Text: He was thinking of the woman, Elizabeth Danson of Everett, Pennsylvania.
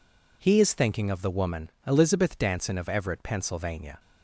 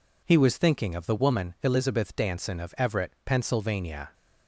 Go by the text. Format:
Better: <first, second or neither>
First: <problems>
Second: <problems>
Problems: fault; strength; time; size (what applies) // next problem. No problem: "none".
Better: second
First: says "is" for "was"; at 0.6 s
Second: none